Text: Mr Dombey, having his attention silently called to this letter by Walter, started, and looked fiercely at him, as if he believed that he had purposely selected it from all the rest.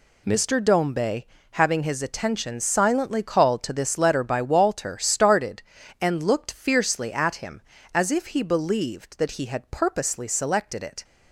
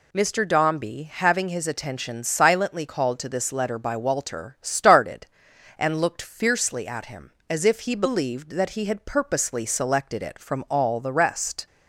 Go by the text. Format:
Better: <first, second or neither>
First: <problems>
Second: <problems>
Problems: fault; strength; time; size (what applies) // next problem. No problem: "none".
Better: second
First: stops before "from all the rest"; at 11.0 s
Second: none